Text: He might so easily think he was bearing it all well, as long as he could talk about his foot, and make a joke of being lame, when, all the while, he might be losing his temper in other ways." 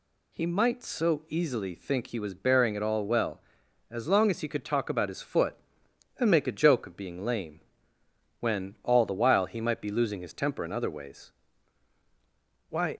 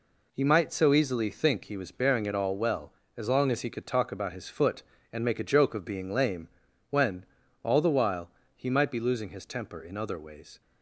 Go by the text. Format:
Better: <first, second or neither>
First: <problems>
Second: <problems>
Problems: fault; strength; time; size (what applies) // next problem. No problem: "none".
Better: second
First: goes on to say "Why"; slight; from 12.7 s on; 0.26 s long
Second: none